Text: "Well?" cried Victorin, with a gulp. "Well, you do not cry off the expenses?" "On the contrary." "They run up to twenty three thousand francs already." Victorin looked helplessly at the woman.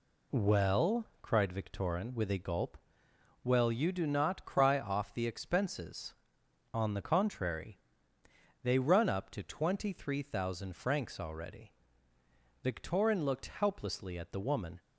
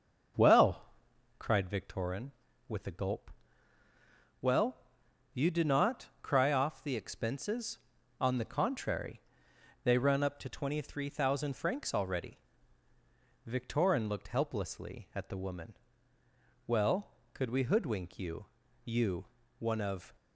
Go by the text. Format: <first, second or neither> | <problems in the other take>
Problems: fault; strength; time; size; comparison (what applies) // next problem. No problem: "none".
first | starts louder than the rest; until 1.8 s; 6.5 dB // goes on to say "Well could we hoodwink you you one of"; strong; from 16.6 s on; 3.4 s long